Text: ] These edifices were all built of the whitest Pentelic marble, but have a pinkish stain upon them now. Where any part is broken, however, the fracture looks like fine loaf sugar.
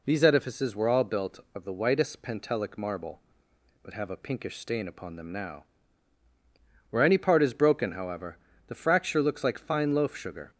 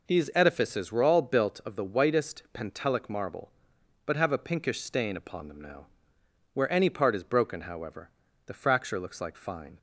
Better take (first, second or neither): first